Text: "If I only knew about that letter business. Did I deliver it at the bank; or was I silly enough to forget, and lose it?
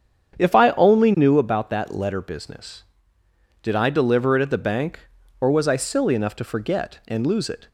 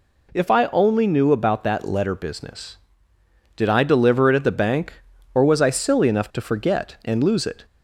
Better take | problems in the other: second | starts louder than the rest; strong; until 1.5 s; 8 dB

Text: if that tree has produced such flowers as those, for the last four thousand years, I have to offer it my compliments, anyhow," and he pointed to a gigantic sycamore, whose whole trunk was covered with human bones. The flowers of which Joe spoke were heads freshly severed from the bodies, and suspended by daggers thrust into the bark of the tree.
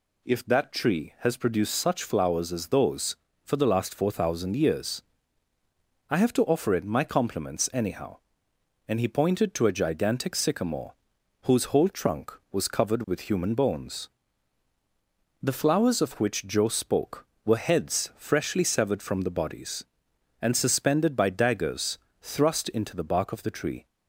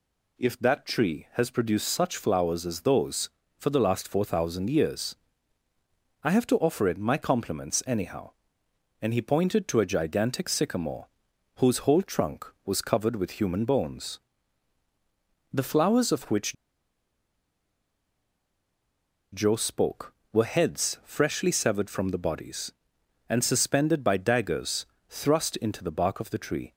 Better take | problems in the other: first | pauses between "which" and "Joe"; strong; at 16.5 s; 2.8 s long // pauses between "daggers" and "thrust"; slight; at 24.8 s; 0.24 s long; slight in the first

